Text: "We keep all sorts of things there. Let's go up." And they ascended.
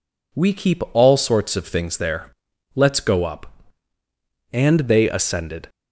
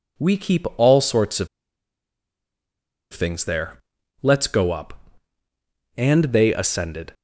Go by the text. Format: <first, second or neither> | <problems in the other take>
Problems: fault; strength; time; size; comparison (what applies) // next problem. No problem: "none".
first | pauses between "of" and "things"; strong; at 1.4 s; 1.6 s long